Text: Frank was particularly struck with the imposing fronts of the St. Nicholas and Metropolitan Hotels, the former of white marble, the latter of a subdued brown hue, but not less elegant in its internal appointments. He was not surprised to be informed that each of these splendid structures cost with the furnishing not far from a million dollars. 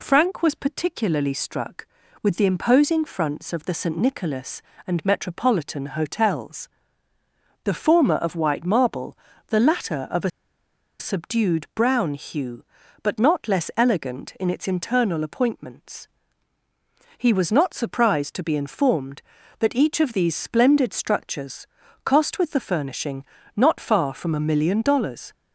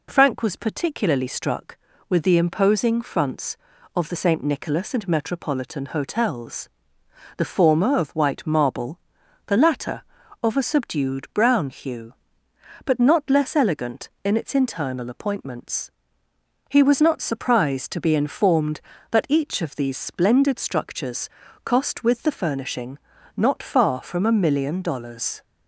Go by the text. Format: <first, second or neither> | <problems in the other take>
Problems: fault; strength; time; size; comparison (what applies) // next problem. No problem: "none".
second | pauses between "a" and "subdued"; noticeable; at 10.2 s; 0.70 s long // pauses between "structures" and "cost"; at 21.6 s; 0.38 s long; slight in the second // pauses between "furnishing" and "not"; slight; at 23.2 s; 0.32 s long; also in the second